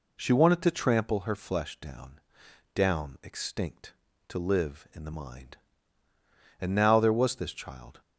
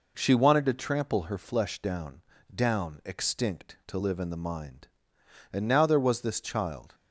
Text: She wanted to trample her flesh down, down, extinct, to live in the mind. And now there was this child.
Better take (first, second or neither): neither